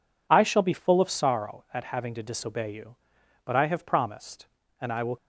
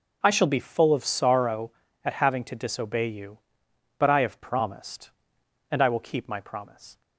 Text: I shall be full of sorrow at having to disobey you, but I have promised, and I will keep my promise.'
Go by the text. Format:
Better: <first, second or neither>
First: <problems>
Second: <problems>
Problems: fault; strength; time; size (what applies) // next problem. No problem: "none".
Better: second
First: stops before "keep my promise"; at 5.1 s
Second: none